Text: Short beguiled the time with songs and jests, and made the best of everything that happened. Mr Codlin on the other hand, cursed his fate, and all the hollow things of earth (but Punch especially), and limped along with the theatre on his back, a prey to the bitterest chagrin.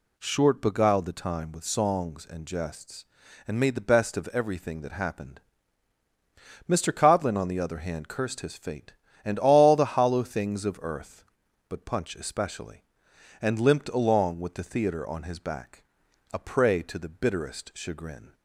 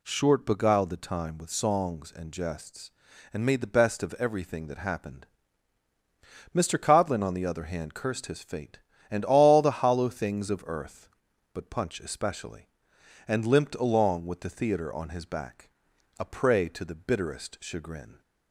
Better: neither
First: none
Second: none

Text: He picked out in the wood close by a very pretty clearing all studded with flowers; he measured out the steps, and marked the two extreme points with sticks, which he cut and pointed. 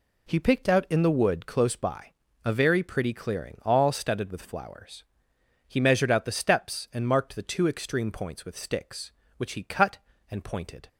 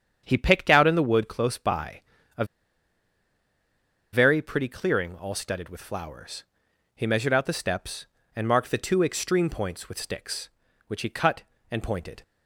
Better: first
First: pauses between "by" and "a"; slight; at 2.1 s; 0.32 s long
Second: starts louder than the rest; strong; until 1.2 s; 8 dB // pauses between "by" and "a"; slight; at 2.0 s; 0.36 s long // pauses between "a" and "very"; strong; at 2.4 s; 1.6 s long

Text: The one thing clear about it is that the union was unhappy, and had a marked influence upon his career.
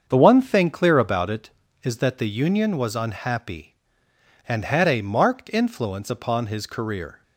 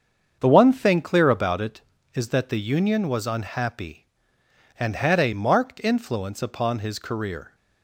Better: neither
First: starts louder than the rest; until 1.0 s; 7 dB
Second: starts louder than the rest; until 1.4 s; 7 dB

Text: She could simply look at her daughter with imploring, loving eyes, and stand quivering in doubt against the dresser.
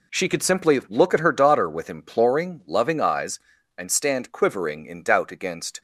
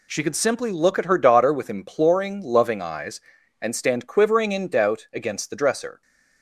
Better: second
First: stops before "the dresser"; at 5.7 s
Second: none

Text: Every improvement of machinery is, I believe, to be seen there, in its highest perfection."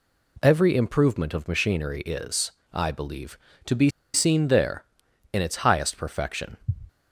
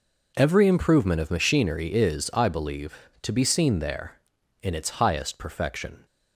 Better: second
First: pauses between "be" and "seen"; slight; at 3.8 s; 0.24 s long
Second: none

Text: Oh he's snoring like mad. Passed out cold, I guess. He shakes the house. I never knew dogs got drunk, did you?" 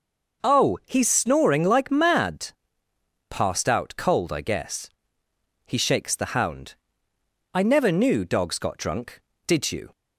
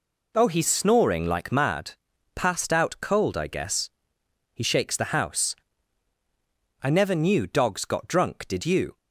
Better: second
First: says "hound" for "house"; at 6.3 s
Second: none

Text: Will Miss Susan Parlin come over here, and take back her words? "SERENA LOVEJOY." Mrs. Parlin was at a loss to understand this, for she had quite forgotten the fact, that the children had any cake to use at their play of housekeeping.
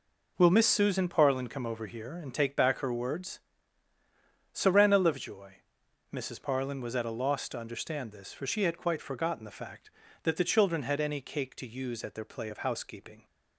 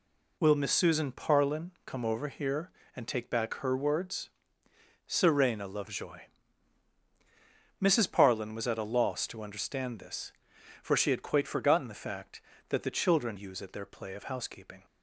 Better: first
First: none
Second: pauses between "Parlin" and "come"; slight; at 1.6 s; 0.16 s long // skips "had any cake to"; at 13.3 s

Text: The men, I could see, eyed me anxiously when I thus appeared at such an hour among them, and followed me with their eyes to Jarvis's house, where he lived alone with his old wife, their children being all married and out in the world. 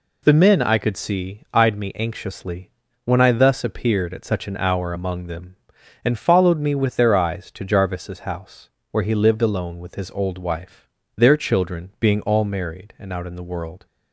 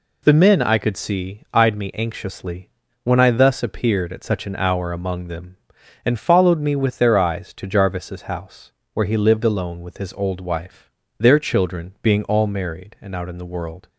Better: neither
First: pauses between "anxiously" and "when"; slight; at 2.6 s; 0.34 s long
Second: pauses between "anxiously" and "when"; slight; at 2.6 s; 0.34 s long

